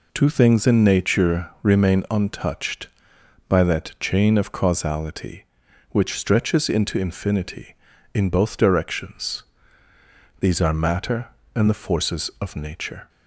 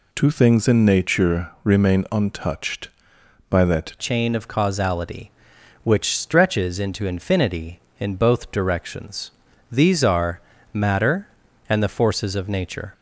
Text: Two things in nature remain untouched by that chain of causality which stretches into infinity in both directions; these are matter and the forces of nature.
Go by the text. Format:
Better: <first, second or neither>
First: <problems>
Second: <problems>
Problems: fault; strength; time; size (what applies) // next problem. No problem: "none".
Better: first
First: none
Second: changes voice at "chain"; from 3.9 s on; 9.0 s long // pauses between "are" and "matter"; slight; at 10.3 s; 0.32 s long